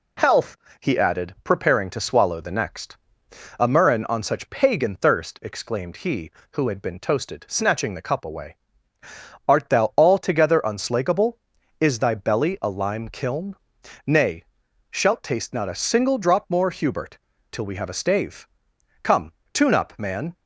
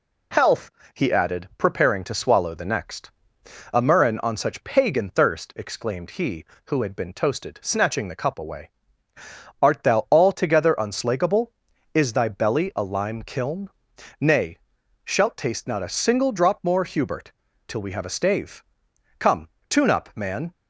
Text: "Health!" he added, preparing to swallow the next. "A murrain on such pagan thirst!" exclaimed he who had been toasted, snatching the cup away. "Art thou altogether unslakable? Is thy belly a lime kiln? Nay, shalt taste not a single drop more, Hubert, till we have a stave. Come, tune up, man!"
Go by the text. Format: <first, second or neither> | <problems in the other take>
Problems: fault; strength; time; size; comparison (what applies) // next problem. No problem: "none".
neither | none